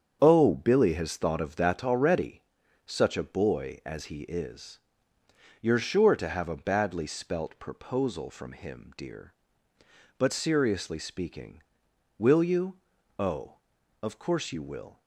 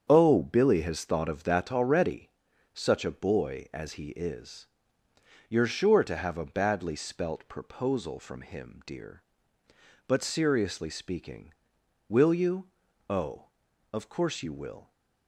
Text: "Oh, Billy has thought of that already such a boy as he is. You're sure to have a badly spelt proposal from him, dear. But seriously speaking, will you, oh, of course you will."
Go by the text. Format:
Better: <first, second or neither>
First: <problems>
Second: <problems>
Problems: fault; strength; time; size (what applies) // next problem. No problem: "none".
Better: neither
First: starts louder than the rest; strong; until 1.2 s; 7.5 dB // pauses between "already" and "such"; at 2.4 s; 0.44 s long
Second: starts louder than the rest; strong; until 1.1 s; 7.5 dB // pauses between "already" and "such"; at 2.2 s; 0.44 s long